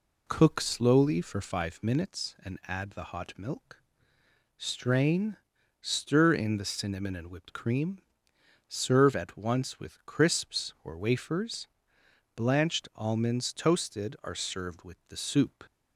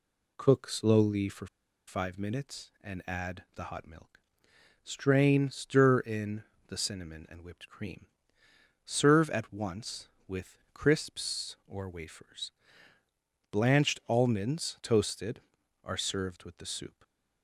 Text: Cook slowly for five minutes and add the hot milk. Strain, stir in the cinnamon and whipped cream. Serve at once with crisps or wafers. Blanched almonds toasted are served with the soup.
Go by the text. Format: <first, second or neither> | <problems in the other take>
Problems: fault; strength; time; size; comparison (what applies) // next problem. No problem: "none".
first | pauses between "for" and "five"; at 1.4 s; 0.41 s long // pauses between "in" and "the"; slight; at 6.4 s; 0.26 s long // pauses between "with" and "crisps"; slight; at 10.5 s; 0.16 s long // stays silent after the last word; slight; from 16.8 s on; 0.6 s long